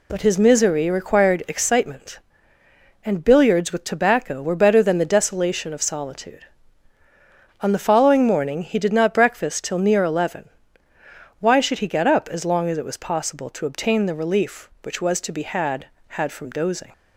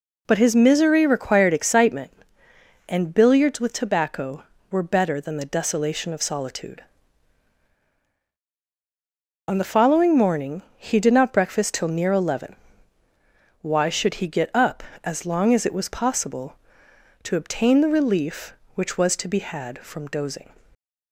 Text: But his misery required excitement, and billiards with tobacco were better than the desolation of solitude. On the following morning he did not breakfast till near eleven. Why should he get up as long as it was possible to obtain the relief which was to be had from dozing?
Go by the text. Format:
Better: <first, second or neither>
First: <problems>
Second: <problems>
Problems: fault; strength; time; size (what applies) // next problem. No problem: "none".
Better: second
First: says "had" twice; at 16.0 s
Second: none